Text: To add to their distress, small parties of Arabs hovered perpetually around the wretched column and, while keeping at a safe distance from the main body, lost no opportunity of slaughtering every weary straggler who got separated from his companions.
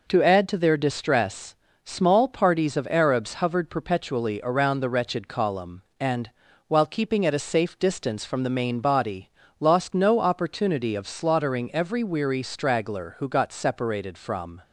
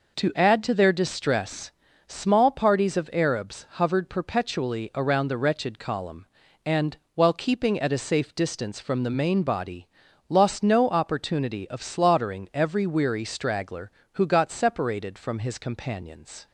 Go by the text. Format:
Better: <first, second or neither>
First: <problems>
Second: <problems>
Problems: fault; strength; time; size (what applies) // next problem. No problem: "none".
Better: second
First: stops before "his companions"; at 14.6 s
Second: none